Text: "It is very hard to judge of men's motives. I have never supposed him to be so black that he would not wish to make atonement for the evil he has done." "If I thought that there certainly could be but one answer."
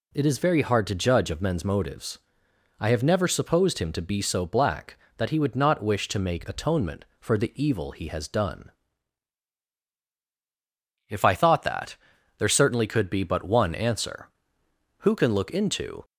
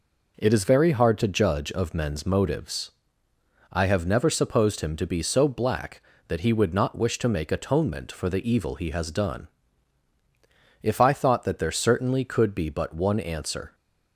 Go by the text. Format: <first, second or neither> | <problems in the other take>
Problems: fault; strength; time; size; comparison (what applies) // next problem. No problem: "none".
second | pauses between "that" and "there"; at 11.9 s; 0.44 s long // goes on to say "Who can look into"; noticeable; from 14.9 s on; 1.0 s long